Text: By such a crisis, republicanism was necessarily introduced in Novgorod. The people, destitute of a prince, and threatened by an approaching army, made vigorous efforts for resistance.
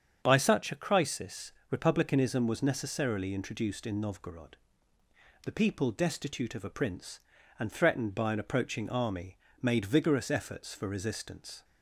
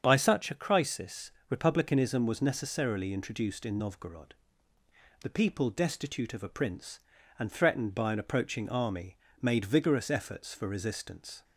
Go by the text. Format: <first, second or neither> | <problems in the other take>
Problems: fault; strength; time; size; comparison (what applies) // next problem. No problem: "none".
neither | starts louder than the rest; strong; the same in both